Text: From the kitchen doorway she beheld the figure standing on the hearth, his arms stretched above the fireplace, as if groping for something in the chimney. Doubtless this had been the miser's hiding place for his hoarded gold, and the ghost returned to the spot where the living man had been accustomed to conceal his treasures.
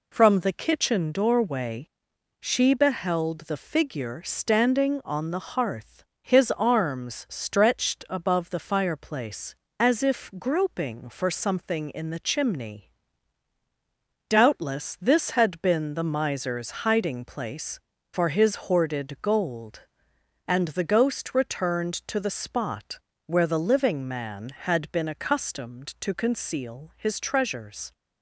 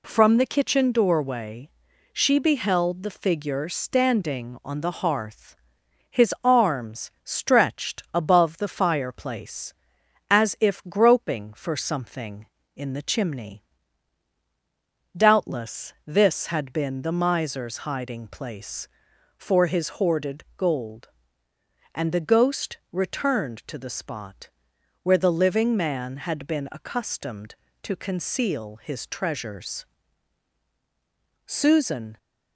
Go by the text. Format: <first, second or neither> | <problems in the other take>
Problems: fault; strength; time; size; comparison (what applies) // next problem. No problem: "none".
first | pauses between "doorway" and "she"; at 1.7 s; 0.42 s long; noticeable in the first // pauses between "spot" and "where"; noticeable; at 24.4 s; 0.52 s long; slight in the first // goes on to say "Susan"; noticeable; from 31.4 s on; 0.70 s long